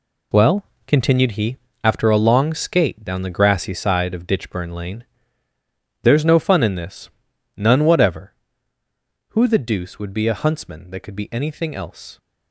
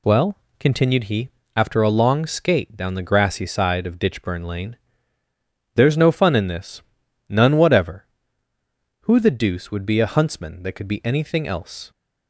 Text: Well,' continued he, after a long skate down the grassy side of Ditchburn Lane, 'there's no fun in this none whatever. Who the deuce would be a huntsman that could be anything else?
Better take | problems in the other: second | gets quieter; strong; throughout; 9 dB // pauses between "this" and "none"; at 7.1 s; 0.44 s long; also in the second

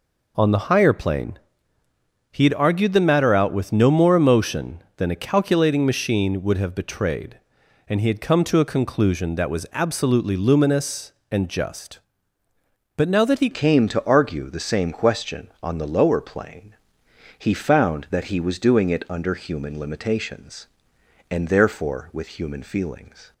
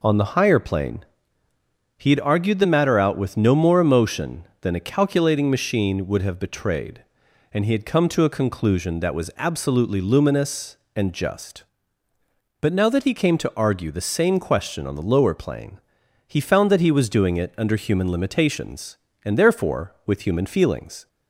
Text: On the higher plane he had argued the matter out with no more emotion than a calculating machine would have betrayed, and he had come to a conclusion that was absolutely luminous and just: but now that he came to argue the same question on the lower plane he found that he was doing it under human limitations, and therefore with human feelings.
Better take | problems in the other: second | pauses between "plane" and "he"; noticeable; at 1.3 s; 0.90 s long; noticeable in the second // changes voice at "came"; from 13.5 s on; 9.8 s long // pauses between "plane" and "he"; noticeable; at 16.7 s; 0.64 s long; noticeable in the second

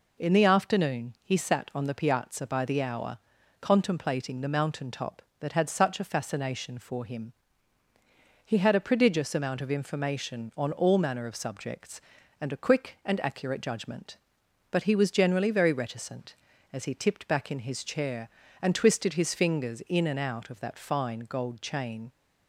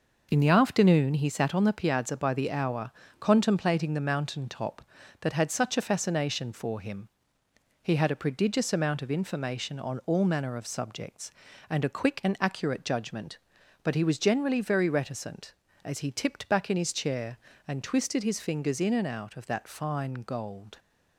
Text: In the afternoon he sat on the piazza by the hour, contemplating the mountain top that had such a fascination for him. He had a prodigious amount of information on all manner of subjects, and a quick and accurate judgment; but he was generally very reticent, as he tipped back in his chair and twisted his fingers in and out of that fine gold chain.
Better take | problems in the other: first | stops before "chain"; at 20.7 s

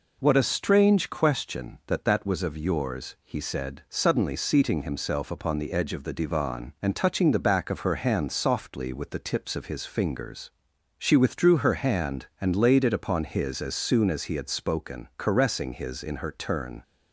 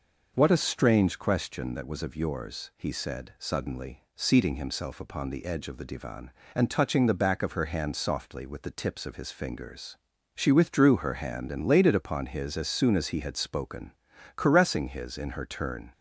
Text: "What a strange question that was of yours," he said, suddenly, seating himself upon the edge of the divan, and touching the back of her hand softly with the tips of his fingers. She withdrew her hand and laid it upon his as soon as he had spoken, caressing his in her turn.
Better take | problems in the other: second | says "that" twice; at 2.0 s

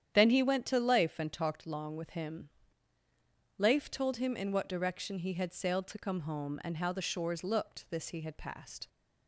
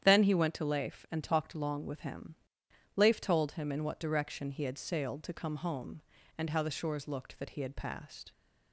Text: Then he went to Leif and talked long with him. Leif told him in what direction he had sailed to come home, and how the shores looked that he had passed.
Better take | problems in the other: second | starts louder than the rest; strong; until 1.1 s; 9.5 dB; strong in the second // says "this" for "that"; at 7.8 s

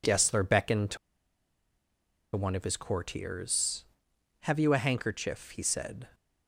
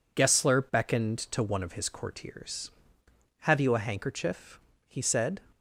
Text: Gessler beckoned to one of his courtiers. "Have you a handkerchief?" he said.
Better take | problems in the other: second | pauses between "to" and "one"; strong; at 0.9 s; 1.3 s long

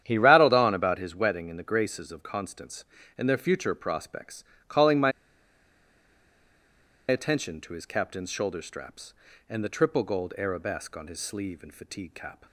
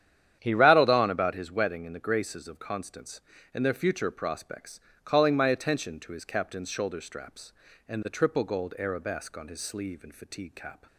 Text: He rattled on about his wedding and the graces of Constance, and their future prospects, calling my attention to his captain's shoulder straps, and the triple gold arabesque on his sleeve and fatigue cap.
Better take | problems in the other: second | starts louder than the rest; strong; until 1.0 s; 10 dB; strong in the second // pauses between "my" and "attention"; strong; at 5.1 s; 1.9 s long

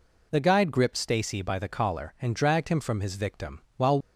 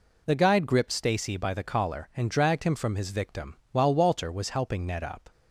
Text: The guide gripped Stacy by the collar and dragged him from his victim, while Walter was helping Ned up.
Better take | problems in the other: second | stops before "Walter was helping Ned up"; at 4.0 s

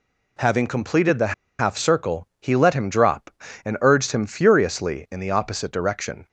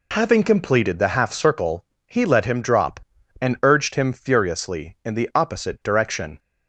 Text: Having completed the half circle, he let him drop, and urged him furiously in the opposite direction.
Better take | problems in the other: second | pauses between "the" and "half"; slight; at 1.3 s; 0.25 s long

